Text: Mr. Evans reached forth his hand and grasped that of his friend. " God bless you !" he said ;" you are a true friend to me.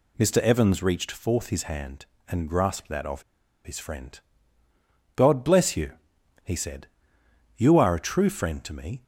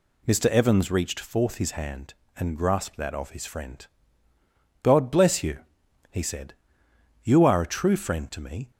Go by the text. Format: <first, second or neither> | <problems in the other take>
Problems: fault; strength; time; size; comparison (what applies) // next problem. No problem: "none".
second | pauses between "of" and "his"; at 3.2 s; 0.42 s long